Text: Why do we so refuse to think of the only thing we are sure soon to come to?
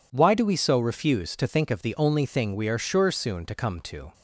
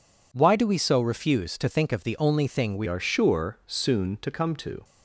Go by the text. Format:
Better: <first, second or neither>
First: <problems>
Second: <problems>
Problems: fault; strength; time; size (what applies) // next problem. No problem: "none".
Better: first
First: none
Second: changes voice at "are"; from 2.8 s on; 2.0 s long